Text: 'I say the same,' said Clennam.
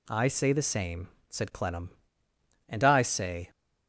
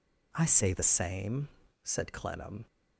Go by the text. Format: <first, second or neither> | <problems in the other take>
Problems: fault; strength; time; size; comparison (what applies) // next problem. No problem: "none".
second | goes on to say "And I say"; noticeable; from 2.6 s on; 0.80 s long